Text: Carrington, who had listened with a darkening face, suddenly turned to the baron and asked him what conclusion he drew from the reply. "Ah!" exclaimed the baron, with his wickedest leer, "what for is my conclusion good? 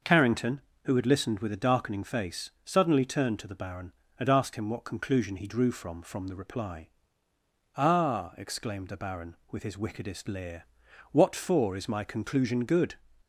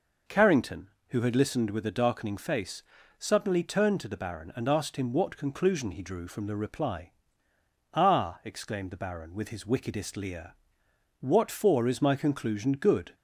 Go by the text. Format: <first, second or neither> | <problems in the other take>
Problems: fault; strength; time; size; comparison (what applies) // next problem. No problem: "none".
second | says "from" twice; at 6.0 s